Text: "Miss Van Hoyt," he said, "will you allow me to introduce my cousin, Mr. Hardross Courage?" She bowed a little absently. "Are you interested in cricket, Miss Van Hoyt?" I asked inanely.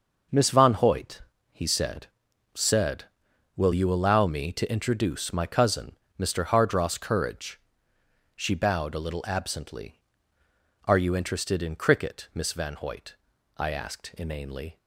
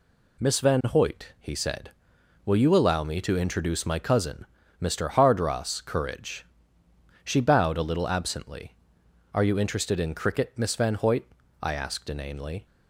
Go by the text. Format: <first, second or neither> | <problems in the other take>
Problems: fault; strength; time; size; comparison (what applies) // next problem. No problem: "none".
second | says "said" twice; at 2.5 s